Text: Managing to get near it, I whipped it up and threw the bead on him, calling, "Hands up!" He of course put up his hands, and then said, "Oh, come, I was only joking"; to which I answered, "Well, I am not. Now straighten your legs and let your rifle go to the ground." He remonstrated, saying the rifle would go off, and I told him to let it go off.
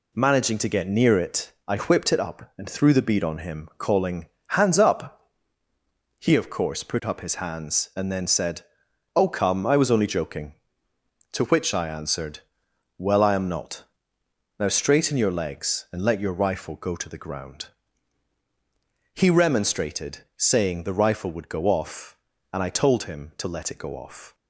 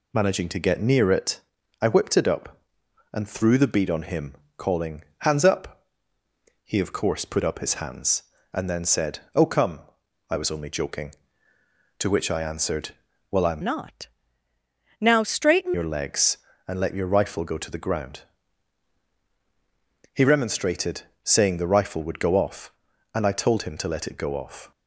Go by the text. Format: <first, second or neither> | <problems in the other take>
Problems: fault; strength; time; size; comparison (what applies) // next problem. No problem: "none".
first | changes voice from "not" to "straighten"; from 13.6 to 15.7 s; 2.1 s long